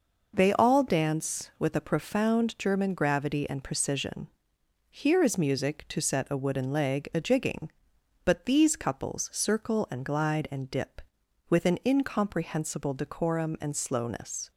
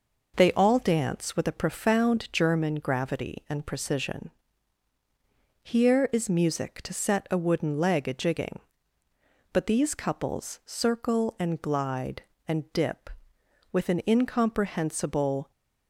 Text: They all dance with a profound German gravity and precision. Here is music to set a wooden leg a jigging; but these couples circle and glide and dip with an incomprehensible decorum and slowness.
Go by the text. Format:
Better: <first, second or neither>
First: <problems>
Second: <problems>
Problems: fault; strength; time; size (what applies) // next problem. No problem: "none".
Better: first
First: none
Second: stops before "decorum and slowness"; at 15.5 s